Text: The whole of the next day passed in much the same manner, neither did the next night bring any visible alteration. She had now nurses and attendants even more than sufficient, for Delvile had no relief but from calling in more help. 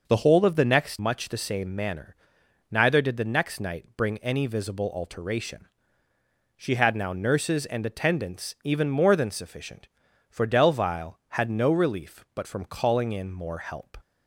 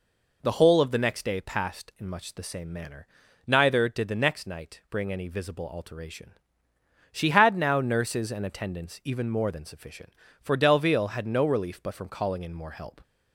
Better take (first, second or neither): second